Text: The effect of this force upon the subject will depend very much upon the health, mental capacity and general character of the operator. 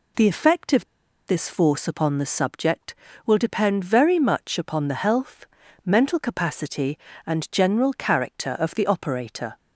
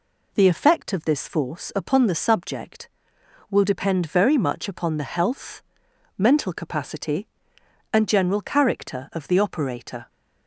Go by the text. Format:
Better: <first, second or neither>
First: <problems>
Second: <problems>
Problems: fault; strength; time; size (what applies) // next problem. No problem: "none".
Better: second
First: pauses between "of" and "this"; at 0.8 s; 0.41 s long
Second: none